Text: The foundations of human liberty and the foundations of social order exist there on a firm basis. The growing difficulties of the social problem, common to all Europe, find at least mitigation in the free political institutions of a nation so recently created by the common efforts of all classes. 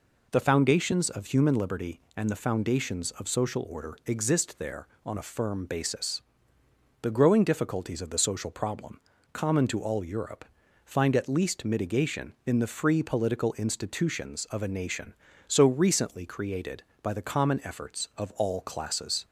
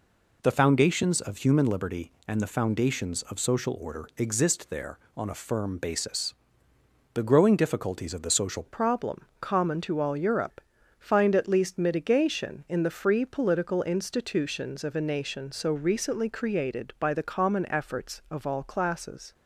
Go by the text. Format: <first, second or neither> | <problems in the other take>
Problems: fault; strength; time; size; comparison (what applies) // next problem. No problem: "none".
first | changes voice at "problem"; from 8.6 s on; 10.7 s long